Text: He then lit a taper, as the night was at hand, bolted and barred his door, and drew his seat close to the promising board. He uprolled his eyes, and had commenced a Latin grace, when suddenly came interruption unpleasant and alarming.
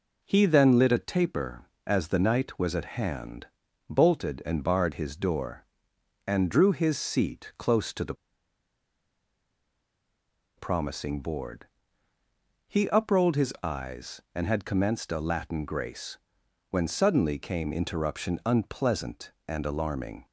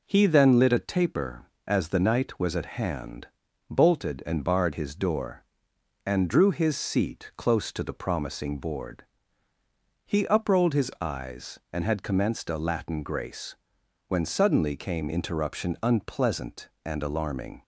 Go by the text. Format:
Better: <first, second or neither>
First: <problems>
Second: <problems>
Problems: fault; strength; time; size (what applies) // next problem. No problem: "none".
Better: second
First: pauses between "the" and "promising"; strong; at 8.1 s; 2.4 s long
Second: none